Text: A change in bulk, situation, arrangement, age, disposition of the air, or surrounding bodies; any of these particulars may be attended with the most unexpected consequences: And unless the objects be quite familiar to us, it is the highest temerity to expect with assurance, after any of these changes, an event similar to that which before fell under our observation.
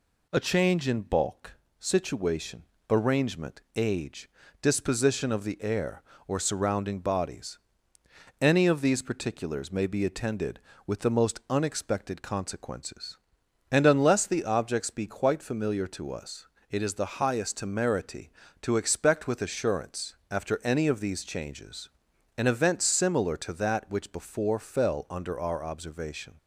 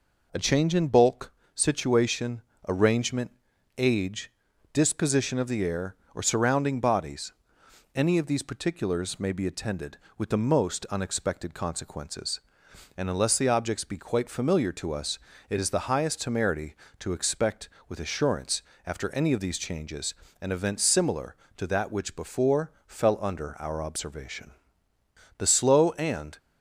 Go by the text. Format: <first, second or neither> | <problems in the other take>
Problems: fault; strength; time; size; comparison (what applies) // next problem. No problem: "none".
first | pauses between "before" and "fell"; slight; at 22.6 s; 0.16 s long // goes on to say "The slow and"; noticeable; from 25.3 s on; 1.0 s long